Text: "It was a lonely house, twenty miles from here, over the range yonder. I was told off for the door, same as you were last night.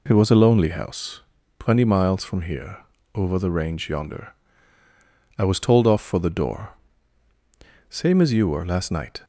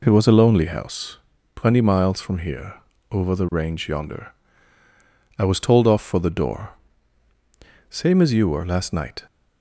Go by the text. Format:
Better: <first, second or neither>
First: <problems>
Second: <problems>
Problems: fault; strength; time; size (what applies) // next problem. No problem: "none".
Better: neither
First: none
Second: none